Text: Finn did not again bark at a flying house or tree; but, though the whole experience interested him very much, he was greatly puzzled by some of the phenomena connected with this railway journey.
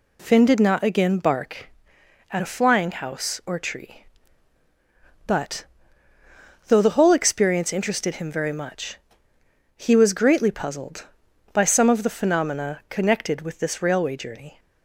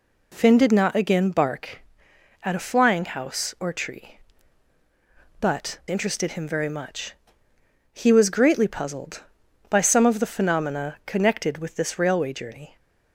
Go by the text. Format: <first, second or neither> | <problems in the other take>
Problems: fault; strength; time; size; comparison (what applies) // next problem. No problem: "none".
first | skips "though the whole experience"; at 5.8 s